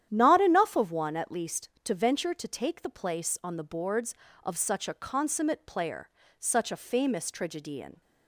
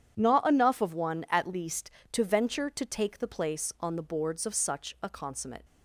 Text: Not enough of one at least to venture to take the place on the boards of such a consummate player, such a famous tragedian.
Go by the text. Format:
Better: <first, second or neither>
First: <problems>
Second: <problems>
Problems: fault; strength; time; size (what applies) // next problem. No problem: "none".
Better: first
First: starts louder than the rest; strong; until 1.1 s; 10 dB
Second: starts louder than the rest; strong; until 1.1 s; 9 dB // stops before "player such a famous tragedian"; at 5.6 s